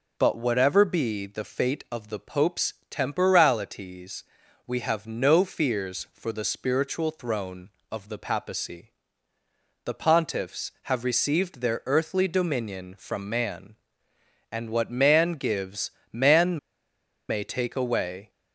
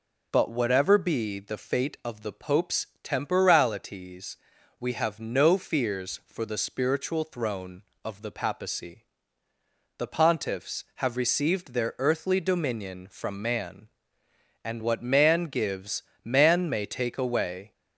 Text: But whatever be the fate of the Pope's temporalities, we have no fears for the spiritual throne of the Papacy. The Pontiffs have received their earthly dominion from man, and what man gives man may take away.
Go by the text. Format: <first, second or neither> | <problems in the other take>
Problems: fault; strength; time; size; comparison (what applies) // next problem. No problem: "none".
second | pauses between "Pope's" and "temporalities"; slight; at 2.7 s; 0.16 s long; slight in the second // pauses between "gives" and "man"; slight; at 15.9 s; 0.20 s long; slight in the second // pauses between "man" and "may"; noticeable; at 16.5 s; 0.72 s long